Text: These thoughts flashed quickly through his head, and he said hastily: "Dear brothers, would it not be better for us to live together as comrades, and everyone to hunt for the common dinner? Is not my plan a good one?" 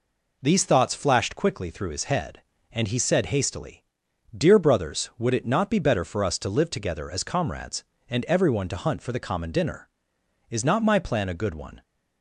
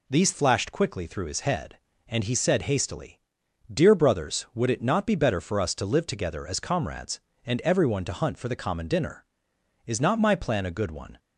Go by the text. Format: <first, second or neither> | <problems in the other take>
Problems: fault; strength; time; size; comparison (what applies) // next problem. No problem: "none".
first | skips "thoughts"; at 0.3 s